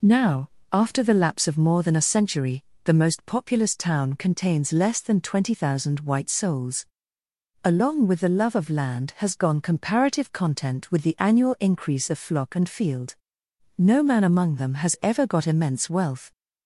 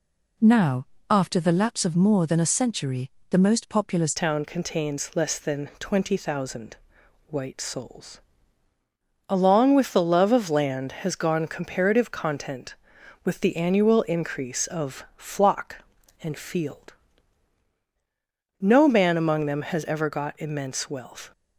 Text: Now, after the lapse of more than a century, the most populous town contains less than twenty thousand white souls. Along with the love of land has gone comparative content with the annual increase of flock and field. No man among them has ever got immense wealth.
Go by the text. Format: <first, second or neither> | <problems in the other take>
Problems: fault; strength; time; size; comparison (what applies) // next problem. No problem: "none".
first | changes voice at "town"; from 4.1 s on; 17.2 s long // pauses between "thousand" and "white"; noticeable; at 6.7 s; 0.52 s long